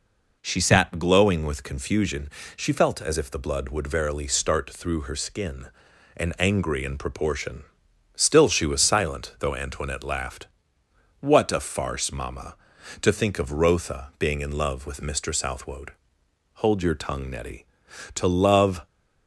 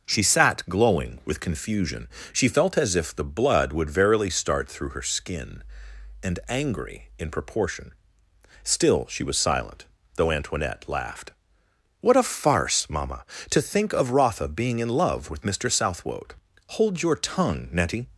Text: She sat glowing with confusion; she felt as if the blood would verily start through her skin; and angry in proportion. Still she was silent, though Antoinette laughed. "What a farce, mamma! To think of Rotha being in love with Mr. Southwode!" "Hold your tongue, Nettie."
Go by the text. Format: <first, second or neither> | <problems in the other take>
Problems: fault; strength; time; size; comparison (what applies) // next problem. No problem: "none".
second | goes on to say "To love"; noticeable; from 18.1 s on; 0.72 s long